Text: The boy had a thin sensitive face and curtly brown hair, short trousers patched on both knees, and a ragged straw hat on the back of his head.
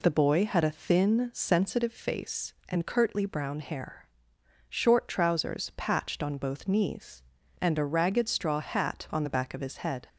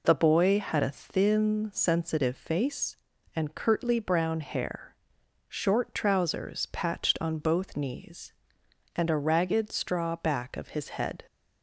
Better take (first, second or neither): first